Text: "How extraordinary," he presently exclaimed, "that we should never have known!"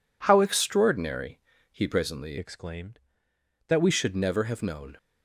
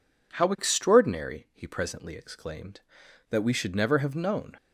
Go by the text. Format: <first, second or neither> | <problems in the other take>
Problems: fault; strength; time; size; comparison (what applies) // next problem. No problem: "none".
second | changes voice from "exclaimed" to "we"; from 2.3 to 3.8 s; 1.5 s long